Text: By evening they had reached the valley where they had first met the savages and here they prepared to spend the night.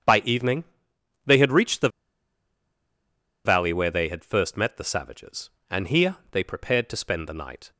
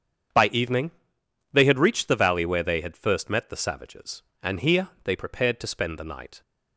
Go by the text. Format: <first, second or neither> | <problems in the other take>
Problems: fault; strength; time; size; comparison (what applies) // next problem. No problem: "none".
second | starts louder than the rest; strong; until 1.6 s; 7.5 dB; strong in the second // pauses between "evening" and "they"; noticeable; at 0.6 s; 0.60 s long; noticeable in the second // pauses between "the" and "valley"; strong; at 1.8 s; 1.5 s long